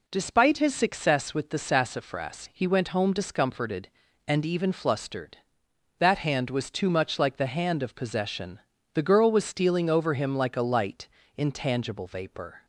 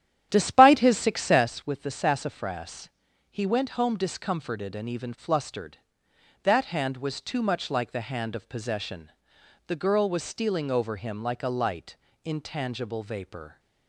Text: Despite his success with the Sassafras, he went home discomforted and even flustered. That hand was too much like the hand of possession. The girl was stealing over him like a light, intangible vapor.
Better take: first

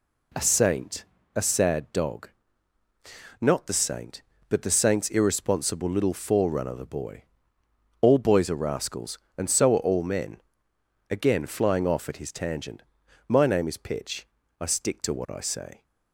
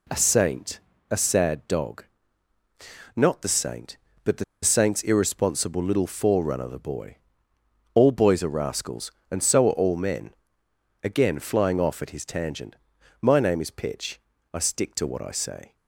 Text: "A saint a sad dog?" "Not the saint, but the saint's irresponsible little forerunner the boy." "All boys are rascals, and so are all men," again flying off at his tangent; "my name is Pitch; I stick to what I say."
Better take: first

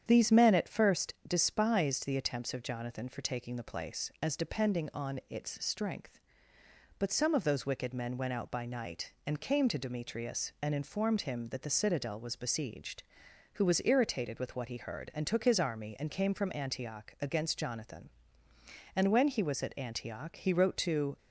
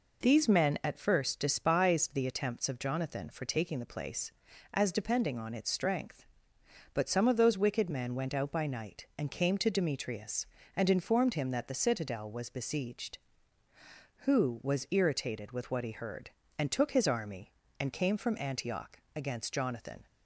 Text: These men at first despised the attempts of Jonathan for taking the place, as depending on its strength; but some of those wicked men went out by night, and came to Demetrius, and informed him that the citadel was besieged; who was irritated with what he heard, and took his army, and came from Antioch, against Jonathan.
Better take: second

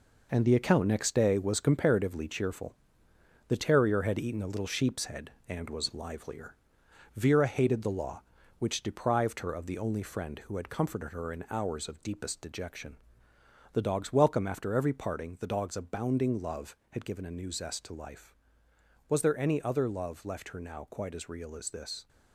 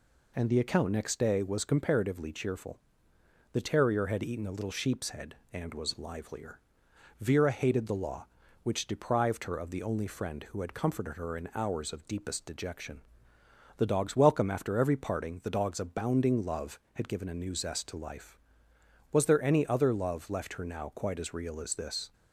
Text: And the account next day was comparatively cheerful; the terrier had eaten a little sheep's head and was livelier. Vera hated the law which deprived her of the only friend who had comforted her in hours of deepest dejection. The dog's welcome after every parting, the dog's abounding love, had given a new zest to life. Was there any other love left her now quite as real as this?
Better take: second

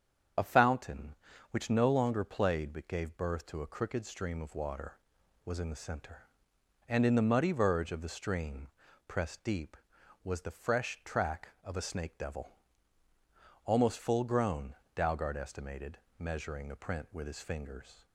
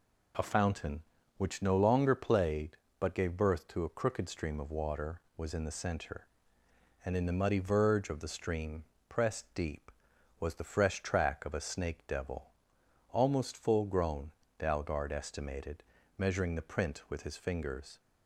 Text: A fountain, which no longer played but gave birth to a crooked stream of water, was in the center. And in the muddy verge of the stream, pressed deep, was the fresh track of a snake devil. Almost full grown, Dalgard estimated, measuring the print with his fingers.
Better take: second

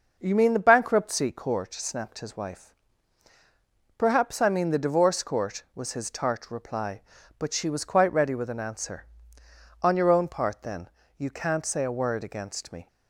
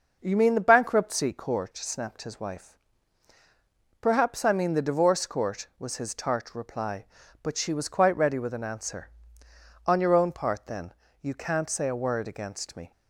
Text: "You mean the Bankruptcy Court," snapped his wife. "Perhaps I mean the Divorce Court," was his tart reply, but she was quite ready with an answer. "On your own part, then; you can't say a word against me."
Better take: neither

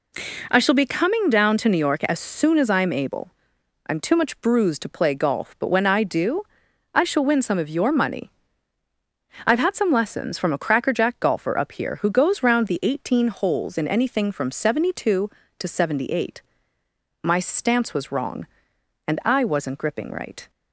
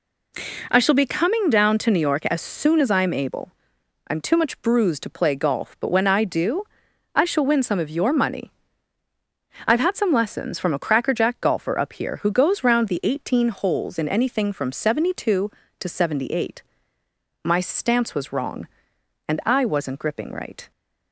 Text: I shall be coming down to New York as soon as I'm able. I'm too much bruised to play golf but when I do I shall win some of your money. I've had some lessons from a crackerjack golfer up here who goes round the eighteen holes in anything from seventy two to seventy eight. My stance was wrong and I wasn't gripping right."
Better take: neither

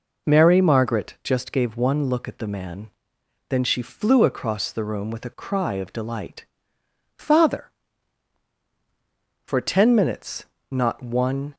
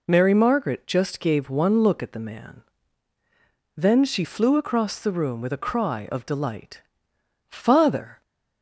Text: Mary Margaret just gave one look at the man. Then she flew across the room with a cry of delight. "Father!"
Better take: second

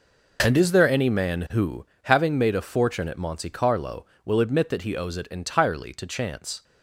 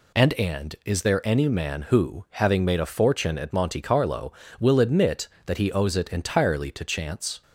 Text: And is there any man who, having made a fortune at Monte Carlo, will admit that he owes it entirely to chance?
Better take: first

